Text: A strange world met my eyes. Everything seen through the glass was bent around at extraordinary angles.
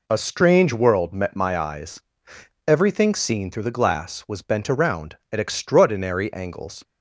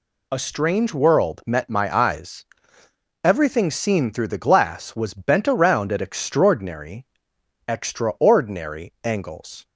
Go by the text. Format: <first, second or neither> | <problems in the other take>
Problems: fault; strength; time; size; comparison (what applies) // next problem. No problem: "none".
first | says "extraordinary" twice; at 7.6 s